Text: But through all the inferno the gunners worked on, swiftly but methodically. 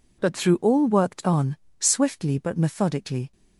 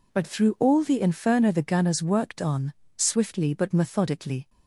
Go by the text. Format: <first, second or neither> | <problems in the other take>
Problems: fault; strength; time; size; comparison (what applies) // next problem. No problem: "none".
second | skips "the inferno the gunners"; at 0.8 s